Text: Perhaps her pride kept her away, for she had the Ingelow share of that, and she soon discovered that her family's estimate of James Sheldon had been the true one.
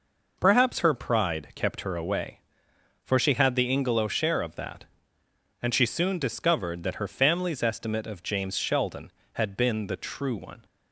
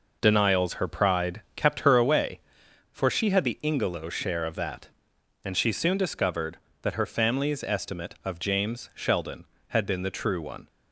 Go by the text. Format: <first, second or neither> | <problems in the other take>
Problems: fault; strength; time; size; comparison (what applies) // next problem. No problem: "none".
first | says "Denials" for "Perhaps"; at 0.2 s